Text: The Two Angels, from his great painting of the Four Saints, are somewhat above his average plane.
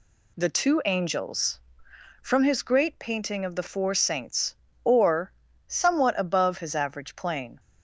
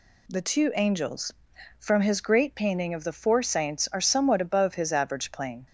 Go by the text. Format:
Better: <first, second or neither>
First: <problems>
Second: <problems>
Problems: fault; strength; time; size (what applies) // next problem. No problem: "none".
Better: second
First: says "or" for "are"; at 4.8 s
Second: none